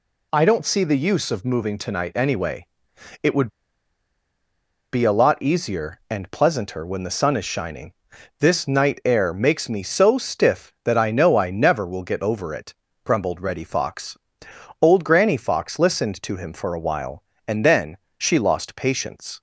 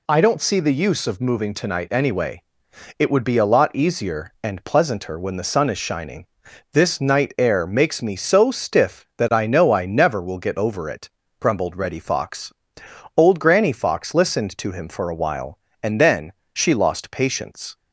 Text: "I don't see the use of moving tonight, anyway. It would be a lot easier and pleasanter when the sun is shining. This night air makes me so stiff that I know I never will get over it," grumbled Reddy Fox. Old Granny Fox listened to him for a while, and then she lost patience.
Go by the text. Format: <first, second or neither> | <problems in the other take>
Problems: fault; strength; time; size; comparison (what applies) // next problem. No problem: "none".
second | pauses between "would" and "be"; strong; at 3.4 s; 1.4 s long // pauses between "then" and "she"; slight; at 17.9 s; 0.22 s long; slight in the second